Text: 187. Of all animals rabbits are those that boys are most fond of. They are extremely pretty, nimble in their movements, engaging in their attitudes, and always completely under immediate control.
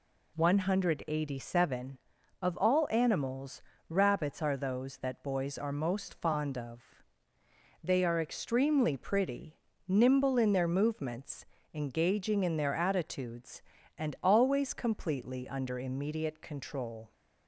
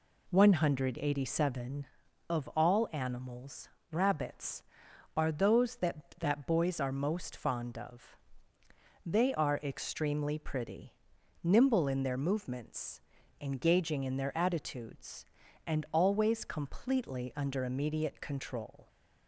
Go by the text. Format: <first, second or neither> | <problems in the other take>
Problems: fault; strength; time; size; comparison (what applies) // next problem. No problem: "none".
first | pauses between "animals" and "rabbits"; slight; at 3.6 s; 0.24 s long; slight in the first // says "that" twice; at 6.1 s